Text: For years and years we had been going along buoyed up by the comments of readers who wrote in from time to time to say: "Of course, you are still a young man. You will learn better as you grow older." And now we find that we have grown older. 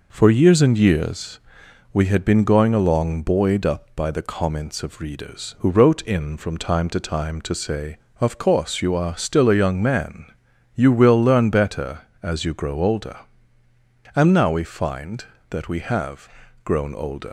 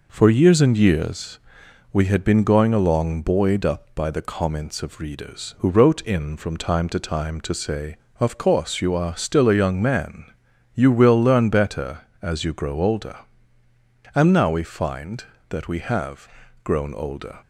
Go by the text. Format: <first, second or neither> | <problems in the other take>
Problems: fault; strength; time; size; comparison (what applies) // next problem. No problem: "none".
second | pauses between "years" and "we"; noticeable; at 1.3 s; 0.54 s long; noticeable in the second // pauses between "have" and "grown"; at 16.2 s; 0.38 s long; also in the second // leaves "older" unfinished; at 17.2 s; 85 ms